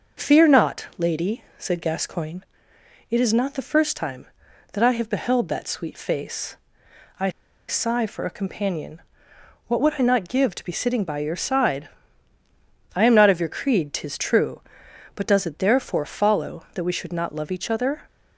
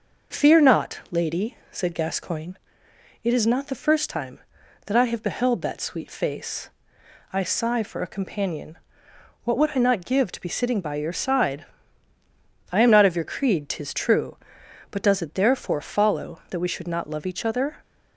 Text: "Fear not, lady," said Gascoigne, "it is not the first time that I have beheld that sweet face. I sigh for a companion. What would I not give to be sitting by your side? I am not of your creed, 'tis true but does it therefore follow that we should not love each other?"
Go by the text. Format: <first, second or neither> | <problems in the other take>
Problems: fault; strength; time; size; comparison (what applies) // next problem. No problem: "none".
second | pauses between "I" and "sigh"; at 7.3 s; 0.38 s long